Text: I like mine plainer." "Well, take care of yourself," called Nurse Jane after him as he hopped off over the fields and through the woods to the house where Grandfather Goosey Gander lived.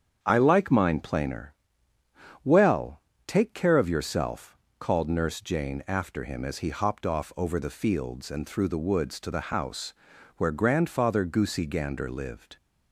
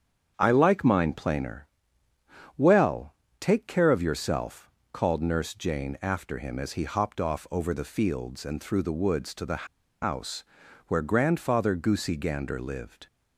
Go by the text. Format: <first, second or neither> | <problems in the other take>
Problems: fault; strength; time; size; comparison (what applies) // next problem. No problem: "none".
first | starts louder than the rest; strong; until 1.3 s; 8 dB; strong in the first // pauses between "the" and "house"; at 9.6 s; 0.37 s long // pauses between "house" and "where"; at 10.4 s; 0.44 s long; also in the first